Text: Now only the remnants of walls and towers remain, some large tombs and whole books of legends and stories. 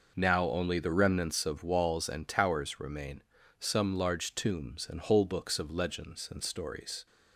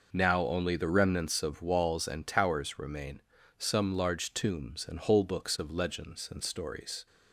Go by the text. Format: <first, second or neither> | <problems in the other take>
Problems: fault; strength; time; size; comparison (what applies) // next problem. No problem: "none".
neither | none